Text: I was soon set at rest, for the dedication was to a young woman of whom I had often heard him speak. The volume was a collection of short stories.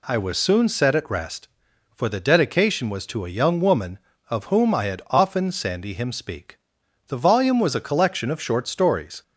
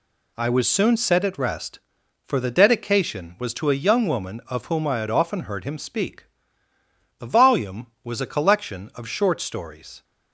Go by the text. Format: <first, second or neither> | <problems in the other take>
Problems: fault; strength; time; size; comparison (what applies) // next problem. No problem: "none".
second | says "sandy" for "heard"; at 5.5 s